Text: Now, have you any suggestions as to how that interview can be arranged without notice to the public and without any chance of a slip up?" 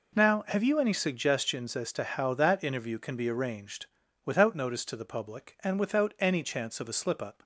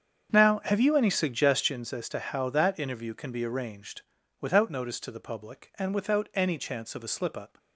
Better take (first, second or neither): first